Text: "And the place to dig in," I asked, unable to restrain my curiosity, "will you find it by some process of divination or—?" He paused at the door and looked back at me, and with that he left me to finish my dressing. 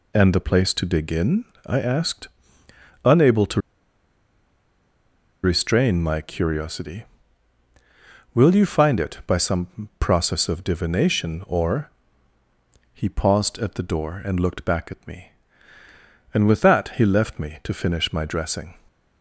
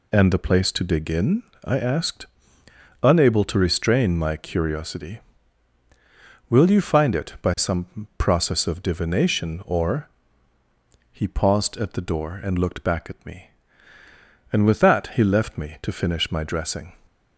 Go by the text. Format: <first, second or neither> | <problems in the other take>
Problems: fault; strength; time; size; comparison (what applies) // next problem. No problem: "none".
second | pauses between "to" and "restrain"; strong; at 3.5 s; 1.8 s long